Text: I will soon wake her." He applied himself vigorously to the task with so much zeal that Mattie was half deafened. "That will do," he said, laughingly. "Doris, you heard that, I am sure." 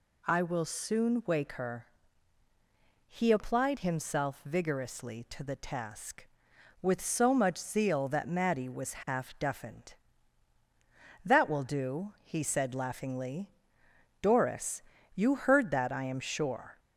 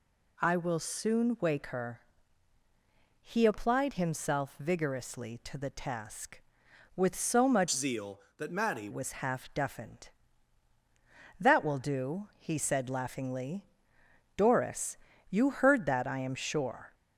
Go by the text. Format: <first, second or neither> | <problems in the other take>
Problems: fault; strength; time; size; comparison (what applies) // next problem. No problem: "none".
first | changes voice from "zeal" to "Mattie"; from 7.7 to 8.8 s; 1.1 s long